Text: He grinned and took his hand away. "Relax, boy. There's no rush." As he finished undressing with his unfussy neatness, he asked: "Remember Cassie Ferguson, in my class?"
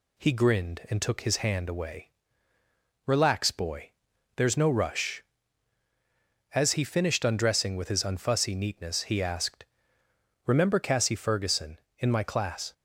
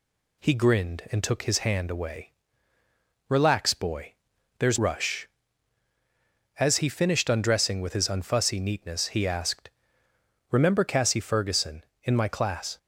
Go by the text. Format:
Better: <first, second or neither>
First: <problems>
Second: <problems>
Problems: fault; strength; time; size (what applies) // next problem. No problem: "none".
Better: first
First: none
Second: skips "no"; at 4.7 s